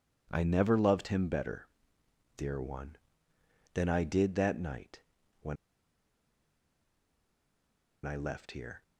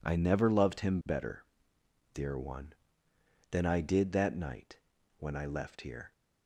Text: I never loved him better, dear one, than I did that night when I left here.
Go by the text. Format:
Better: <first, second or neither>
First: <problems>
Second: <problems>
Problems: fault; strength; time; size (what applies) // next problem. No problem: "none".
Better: second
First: pauses between "night" and "when"; at 5.0 s; 0.40 s long // pauses between "when" and "I"; strong; at 5.5 s; 2.5 s long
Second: pauses between "night" and "when"; at 4.7 s; 0.40 s long